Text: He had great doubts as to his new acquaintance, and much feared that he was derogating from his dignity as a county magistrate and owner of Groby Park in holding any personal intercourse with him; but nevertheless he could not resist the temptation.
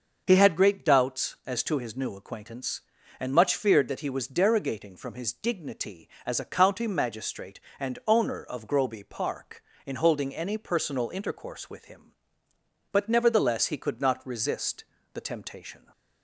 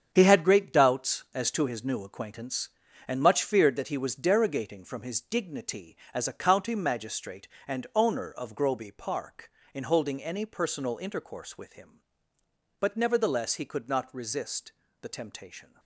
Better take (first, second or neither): first